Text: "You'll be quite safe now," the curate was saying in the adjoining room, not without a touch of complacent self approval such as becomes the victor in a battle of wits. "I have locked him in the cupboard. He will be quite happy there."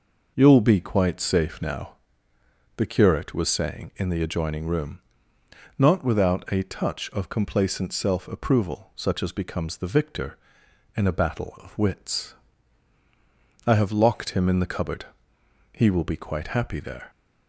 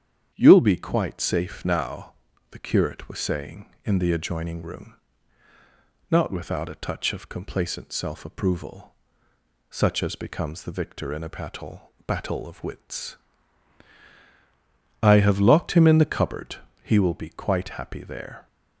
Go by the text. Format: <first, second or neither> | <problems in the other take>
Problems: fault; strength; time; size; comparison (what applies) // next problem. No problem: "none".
first | starts louder than the rest; strong; until 1.3 s; 8.5 dB // pauses between "approval" and "such"; noticeable; at 8.9 s; 0.74 s long // says "battle" twice; at 12.0 s